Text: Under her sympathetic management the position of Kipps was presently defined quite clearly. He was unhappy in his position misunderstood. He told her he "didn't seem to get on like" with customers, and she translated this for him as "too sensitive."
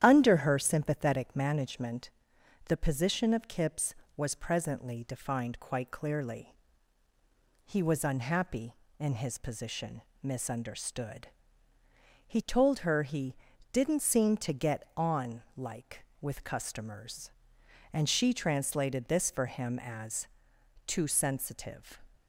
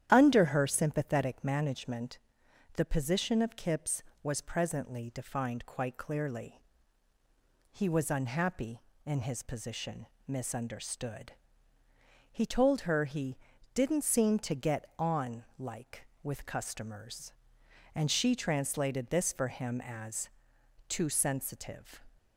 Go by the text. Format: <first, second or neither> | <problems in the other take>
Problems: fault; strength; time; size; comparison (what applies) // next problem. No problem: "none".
neither | starts louder than the rest; strong; the same in both // pauses between "management" and "the"; noticeable; the same in both // pauses between "position" and "misunderstood"; slight; the same in both // pauses between "he" and "didn't"; the same in both // pauses between "on" and "like"; slight; the same in both // pauses between "as" and "too"; noticeable; the same in both